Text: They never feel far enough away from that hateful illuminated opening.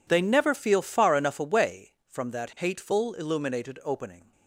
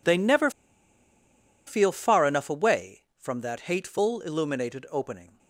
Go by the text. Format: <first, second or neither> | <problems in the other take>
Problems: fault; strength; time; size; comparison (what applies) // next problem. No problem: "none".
first | pauses between "never" and "feel"; at 0.5 s; 1.1 s long